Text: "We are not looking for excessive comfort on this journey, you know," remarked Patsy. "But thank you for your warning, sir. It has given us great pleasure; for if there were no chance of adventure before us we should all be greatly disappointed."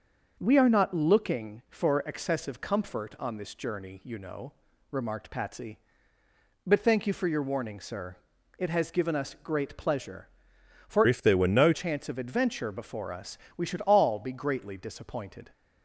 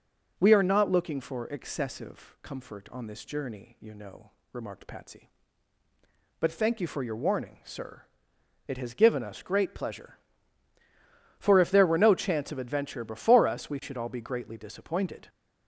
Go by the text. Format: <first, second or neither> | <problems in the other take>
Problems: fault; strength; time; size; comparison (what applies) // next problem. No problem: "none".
second | starts louder than the rest; until 1.4 s; 6.5 dB // changes voice from "if" to "no"; from 11.0 to 11.7 s; 0.7 s long // pauses between "us" and "we"; slight; at 13.3 s; 0.16 s long